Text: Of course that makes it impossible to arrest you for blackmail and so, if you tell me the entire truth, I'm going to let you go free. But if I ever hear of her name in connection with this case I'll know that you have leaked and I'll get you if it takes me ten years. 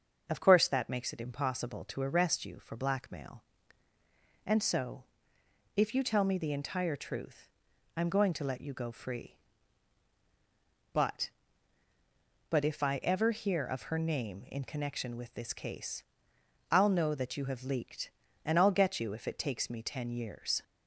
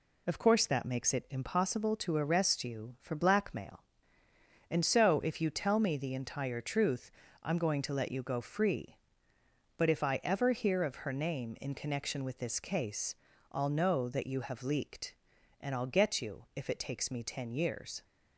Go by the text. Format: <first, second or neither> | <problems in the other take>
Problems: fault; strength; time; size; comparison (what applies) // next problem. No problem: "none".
second | says "But" twice; at 12.4 s // pauses between "case" and "I'll"; noticeable; at 16.0 s; 0.68 s long; slight in the second